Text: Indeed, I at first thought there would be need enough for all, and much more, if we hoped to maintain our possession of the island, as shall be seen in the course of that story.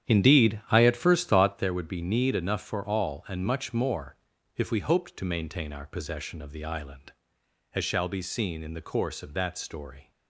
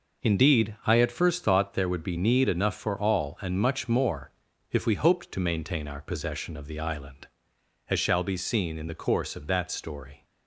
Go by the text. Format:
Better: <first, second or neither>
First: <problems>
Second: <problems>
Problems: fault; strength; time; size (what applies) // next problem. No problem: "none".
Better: second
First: starts louder than the rest; strong; until 1.8 s; 10 dB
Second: none